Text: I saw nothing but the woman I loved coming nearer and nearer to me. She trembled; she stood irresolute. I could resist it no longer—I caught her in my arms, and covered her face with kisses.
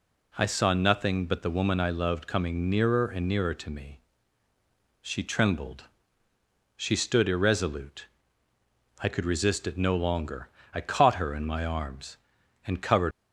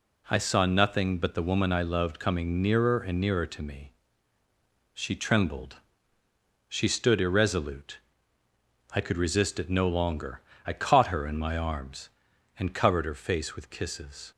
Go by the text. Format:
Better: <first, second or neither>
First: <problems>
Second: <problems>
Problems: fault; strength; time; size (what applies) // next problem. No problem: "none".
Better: second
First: stops before "her face with kisses"; at 13.1 s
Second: none